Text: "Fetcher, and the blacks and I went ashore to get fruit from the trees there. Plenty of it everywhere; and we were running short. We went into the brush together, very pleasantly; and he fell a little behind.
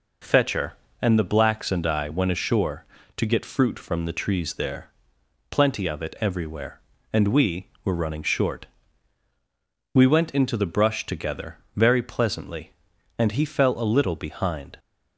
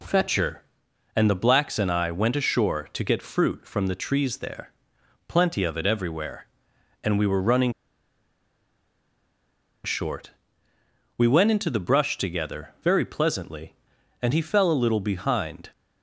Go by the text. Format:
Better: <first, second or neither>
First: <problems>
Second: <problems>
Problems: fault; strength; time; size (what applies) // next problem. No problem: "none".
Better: first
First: none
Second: pauses between "running" and "short"; strong; at 7.7 s; 2.1 s long